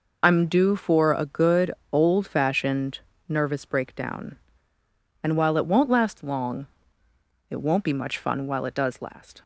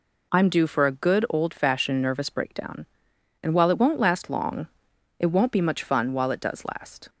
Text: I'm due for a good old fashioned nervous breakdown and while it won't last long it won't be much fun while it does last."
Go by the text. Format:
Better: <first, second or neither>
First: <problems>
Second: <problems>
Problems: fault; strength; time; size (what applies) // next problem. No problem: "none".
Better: second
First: loses the start of "I'm"; at 0.2 s; 30 ms // pauses between "good" and "old"; slight; at 1.7 s; 0.20 s long // pauses between "fashioned" and "nervous"; slight; at 2.9 s; 0.30 s long // pauses between "long" and "it"; noticeable; at 6.6 s; 0.84 s long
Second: pauses between "long" and "it"; noticeable; at 4.6 s; 0.52 s long